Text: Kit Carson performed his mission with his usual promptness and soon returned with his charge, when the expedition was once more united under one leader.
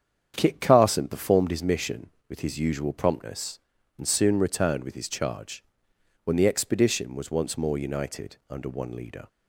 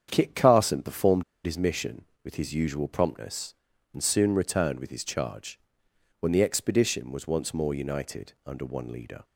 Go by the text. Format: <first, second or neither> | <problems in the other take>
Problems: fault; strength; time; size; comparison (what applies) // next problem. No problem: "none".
first | starts louder than the rest; strong; until 1.1 s; 8 dB; strong in the first // pauses between "performed" and "his"; slight; at 1.2 s; 0.22 s long